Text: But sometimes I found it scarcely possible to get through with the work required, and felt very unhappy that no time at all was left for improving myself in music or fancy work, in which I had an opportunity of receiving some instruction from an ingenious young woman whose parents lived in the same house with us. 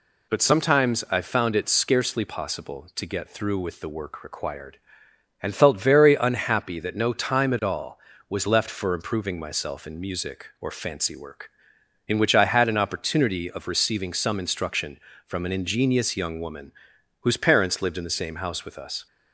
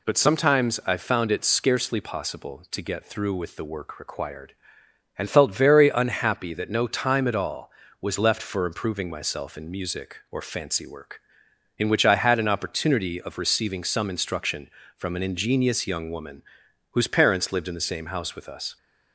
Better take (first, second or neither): neither